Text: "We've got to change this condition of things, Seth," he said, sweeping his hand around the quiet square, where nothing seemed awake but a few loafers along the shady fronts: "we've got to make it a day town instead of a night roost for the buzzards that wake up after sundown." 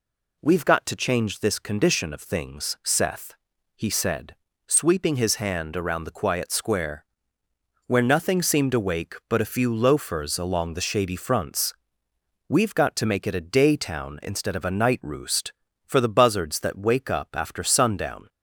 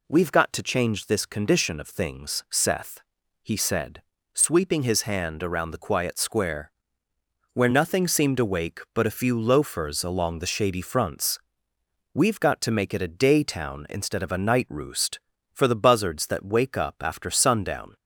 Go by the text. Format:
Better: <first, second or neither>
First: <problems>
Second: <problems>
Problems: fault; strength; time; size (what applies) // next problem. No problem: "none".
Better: neither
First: none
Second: none